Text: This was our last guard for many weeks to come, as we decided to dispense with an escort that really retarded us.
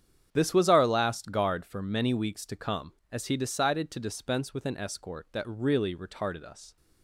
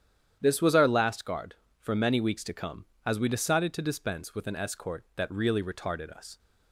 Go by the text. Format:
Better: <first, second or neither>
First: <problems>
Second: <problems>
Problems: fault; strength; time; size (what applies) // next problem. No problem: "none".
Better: second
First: starts louder than the rest; strong; until 1.3 s; 8.5 dB // says "he" for "we"; at 3.2 s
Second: starts louder than the rest; strong; until 1.4 s; 9.5 dB